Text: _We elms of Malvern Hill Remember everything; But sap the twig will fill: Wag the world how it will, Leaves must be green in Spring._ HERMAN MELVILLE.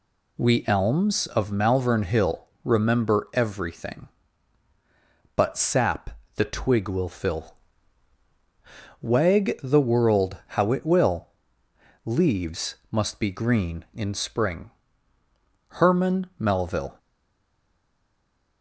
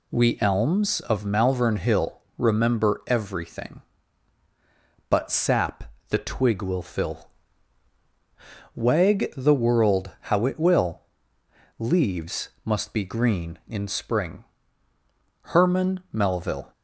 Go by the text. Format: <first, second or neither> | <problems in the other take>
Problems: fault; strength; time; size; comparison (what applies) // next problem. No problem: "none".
second | pauses between "Hill" and "Remember"; slight; at 2.4 s; 0.18 s long; slight in the second // pauses between "sap" and "the"; slight; at 6.0 s; 0.24 s long; slight in the second // pauses between "Leaves" and "must"; slight; at 12.7 s; 0.16 s long; slight in the second // stays silent after the last word; noticeable; from 16.9 s on; 1.7 s long